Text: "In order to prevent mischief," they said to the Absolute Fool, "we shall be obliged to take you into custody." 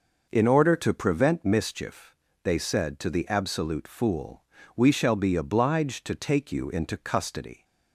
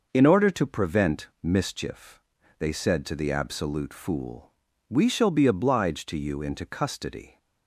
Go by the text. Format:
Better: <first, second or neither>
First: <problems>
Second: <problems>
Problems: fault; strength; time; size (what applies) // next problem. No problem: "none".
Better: first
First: none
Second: pauses between "prevent" and "mischief"; slight; at 1.2 s; 0.16 s long // skips "take"; at 6.1 s